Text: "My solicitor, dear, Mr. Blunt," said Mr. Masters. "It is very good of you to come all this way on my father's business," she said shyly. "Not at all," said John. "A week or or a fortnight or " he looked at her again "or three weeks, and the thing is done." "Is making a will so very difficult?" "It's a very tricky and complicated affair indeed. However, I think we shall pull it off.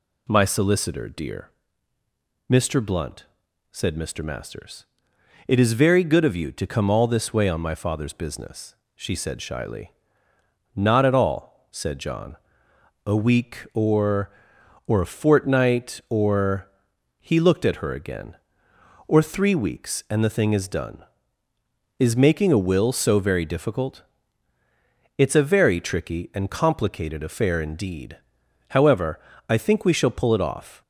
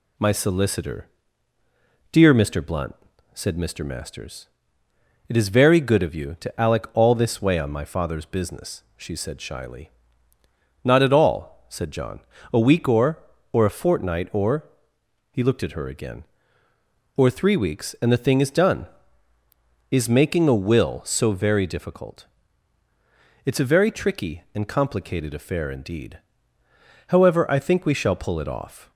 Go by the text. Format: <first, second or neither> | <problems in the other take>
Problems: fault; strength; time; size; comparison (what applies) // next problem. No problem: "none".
first | says "alec" for "come"; at 6.6 s